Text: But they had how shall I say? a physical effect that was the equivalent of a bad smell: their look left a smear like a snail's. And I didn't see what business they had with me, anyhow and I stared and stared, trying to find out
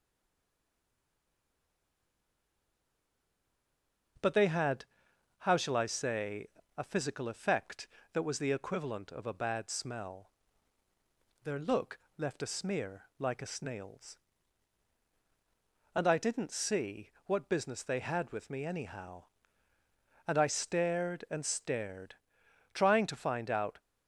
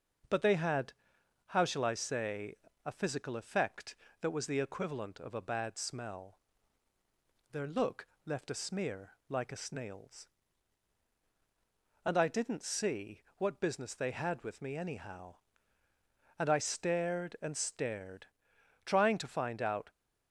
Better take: second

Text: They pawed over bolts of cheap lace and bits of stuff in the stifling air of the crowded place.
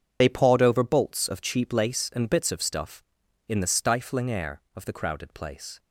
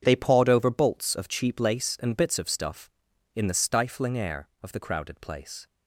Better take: second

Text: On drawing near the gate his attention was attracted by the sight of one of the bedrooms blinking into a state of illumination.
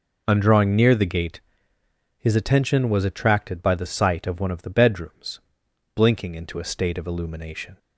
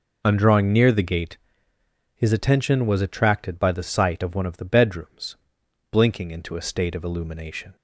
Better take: neither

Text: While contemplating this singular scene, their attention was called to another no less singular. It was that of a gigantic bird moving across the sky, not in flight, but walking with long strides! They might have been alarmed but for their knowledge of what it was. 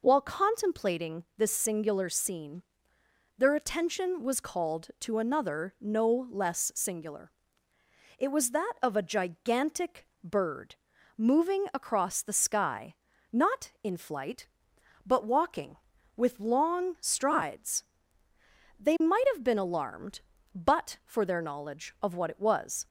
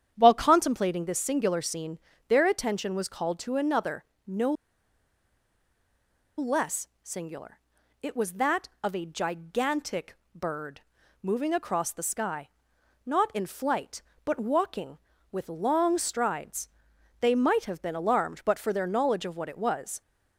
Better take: first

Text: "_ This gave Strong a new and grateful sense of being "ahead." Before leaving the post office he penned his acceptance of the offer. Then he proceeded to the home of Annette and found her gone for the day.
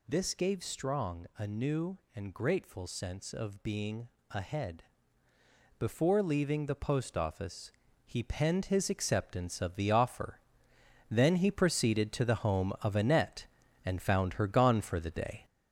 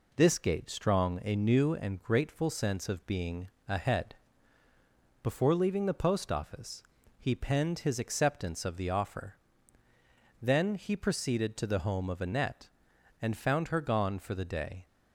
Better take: second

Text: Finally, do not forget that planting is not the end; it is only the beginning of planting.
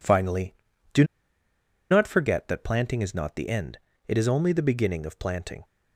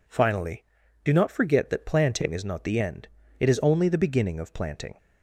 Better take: second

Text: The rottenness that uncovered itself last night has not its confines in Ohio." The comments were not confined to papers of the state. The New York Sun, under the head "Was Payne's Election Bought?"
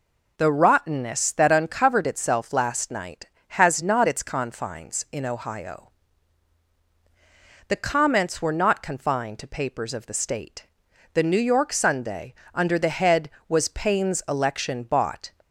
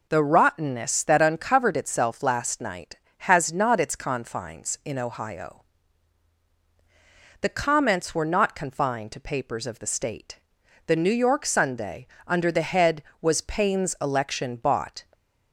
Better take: neither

